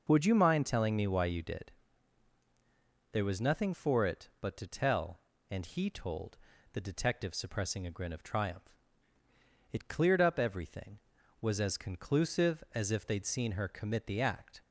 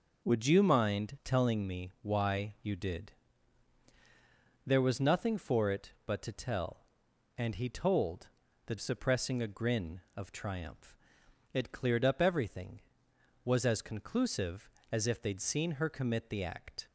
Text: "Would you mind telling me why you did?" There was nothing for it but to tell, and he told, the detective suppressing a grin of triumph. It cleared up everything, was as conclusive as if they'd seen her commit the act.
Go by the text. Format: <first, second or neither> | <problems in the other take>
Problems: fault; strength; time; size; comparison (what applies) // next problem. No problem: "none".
first | skips "detective"; at 8.7 s